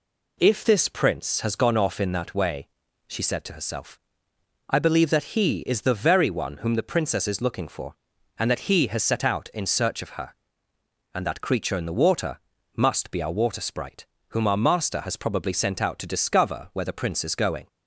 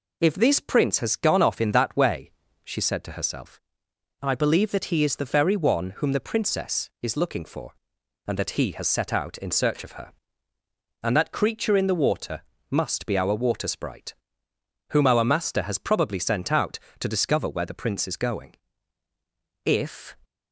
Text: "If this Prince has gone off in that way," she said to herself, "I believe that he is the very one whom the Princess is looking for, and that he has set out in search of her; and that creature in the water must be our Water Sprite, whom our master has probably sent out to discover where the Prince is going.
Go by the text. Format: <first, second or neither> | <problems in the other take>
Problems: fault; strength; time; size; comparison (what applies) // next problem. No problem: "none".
first | pauses between "water" and "must"; slight; at 12.4 s; 0.28 s long; also in the first // goes on to say "If"; from 19.6 s on; 0.50 s long